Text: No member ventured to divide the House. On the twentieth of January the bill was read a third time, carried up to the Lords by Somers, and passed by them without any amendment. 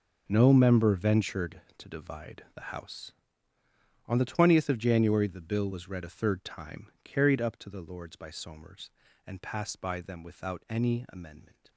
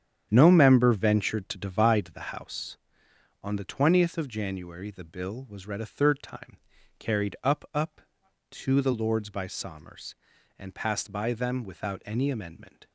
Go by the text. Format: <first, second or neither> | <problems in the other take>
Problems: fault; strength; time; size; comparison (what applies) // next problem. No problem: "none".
first | starts louder than the rest; strong; until 1.3 s; 9 dB // says "up" twice; at 7.7 s